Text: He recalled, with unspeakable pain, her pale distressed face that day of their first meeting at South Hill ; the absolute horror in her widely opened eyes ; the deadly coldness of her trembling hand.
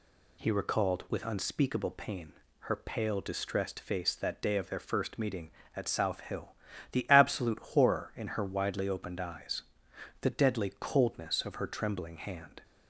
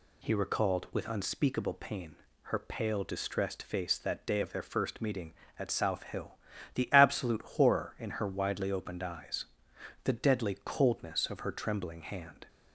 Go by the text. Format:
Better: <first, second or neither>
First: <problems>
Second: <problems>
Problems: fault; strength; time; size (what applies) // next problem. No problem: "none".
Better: neither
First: none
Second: none